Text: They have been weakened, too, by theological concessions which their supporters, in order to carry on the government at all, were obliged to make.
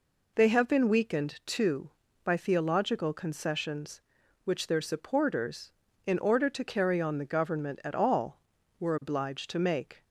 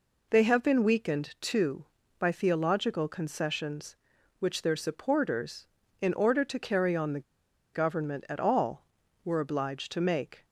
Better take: first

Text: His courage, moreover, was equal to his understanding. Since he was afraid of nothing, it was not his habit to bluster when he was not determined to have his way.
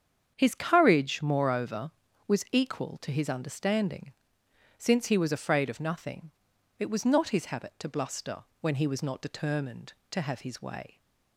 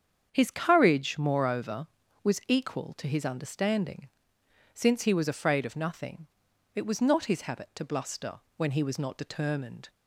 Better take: first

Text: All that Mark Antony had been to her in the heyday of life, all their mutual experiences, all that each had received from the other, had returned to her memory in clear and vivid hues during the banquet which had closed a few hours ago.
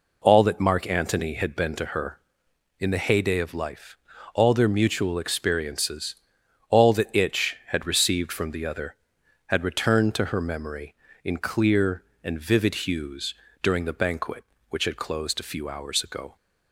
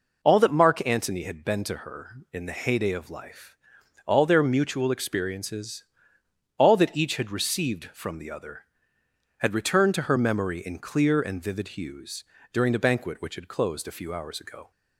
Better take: second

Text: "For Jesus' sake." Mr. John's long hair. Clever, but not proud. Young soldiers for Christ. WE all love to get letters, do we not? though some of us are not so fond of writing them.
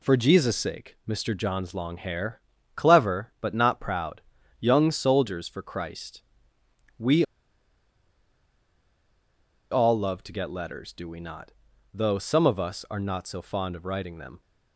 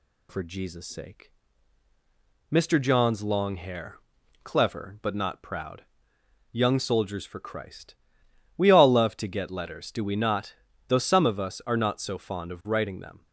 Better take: second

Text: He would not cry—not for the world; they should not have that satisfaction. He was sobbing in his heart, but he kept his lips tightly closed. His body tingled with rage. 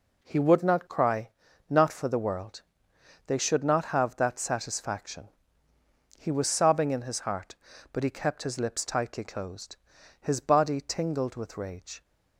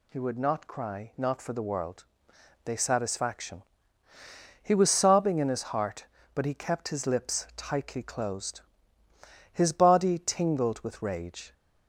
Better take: first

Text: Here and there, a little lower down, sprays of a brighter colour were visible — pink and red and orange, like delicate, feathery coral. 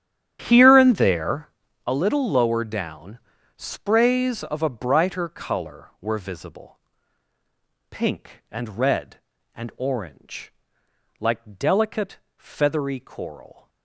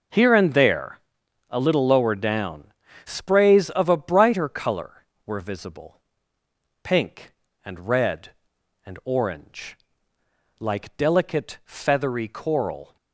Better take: second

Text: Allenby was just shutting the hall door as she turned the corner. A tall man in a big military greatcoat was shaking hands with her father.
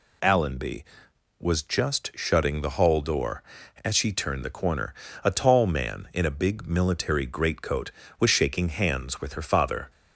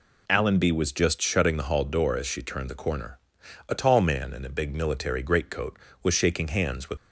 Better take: first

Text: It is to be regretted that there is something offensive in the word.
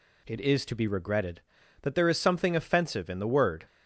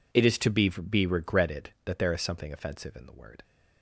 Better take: first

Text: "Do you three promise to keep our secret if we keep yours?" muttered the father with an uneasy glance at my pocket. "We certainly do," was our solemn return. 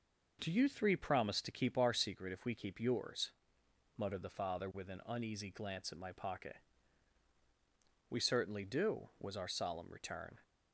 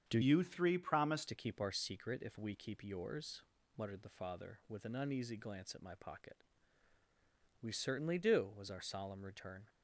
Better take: first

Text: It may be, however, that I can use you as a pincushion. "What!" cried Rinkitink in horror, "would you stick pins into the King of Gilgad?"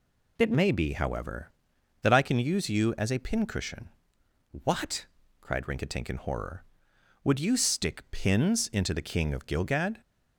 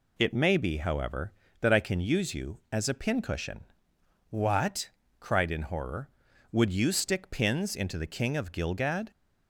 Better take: first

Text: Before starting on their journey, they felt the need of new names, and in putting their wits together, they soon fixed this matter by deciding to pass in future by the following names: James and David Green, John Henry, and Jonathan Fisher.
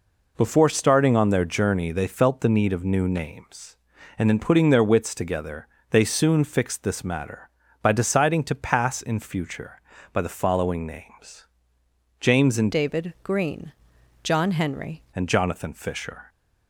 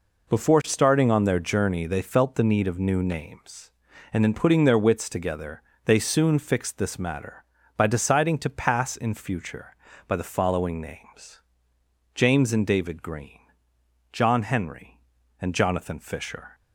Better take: second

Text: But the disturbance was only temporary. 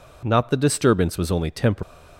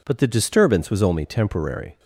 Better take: second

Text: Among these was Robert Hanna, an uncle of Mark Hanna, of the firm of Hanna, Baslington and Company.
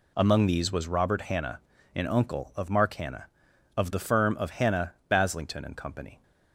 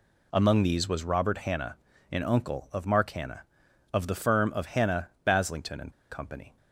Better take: first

